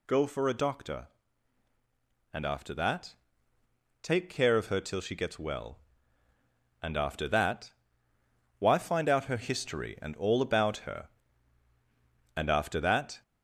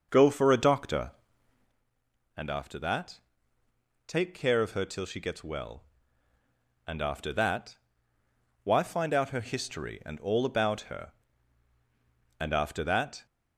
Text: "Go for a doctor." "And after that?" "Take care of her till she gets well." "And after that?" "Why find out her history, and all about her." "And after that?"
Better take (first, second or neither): first